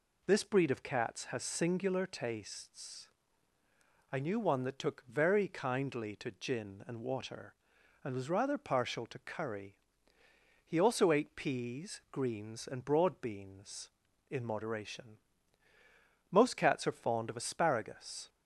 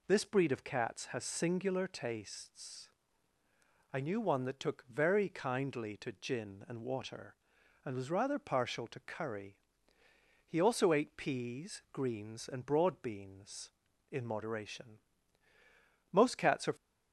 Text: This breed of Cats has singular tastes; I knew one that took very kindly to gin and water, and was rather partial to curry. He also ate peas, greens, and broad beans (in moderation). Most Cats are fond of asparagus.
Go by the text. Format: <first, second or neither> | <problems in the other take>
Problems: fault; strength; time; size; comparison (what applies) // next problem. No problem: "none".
first | stops before "fond of asparagus"; at 16.7 s